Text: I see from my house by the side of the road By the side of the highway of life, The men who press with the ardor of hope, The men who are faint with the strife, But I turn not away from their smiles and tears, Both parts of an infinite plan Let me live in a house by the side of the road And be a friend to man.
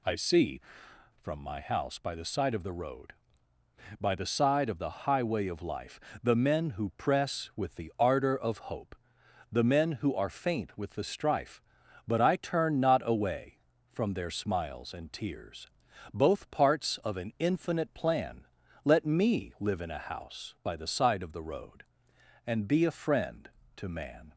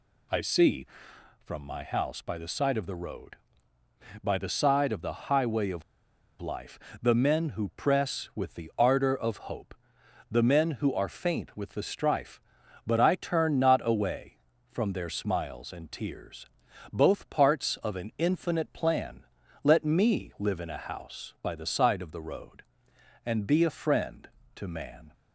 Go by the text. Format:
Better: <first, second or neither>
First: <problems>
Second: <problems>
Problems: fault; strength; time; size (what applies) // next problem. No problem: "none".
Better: first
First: pauses between "plan" and "Let"; at 18.4 s; 0.38 s long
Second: pauses between "of" and "life"; noticeable; at 5.8 s; 0.57 s long // pauses between "plan" and "Let"; at 19.2 s; 0.38 s long